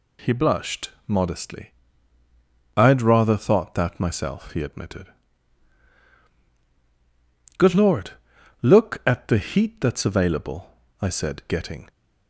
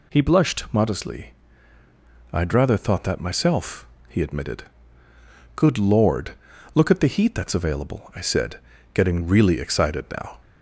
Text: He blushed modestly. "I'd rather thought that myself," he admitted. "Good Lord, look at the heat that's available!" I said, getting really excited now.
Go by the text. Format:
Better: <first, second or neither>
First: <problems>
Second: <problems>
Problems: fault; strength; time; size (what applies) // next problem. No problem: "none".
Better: second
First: pauses between "blushed" and "modestly"; slight; at 0.8 s; 0.18 s long // stops before "really excited now"; at 11.8 s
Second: none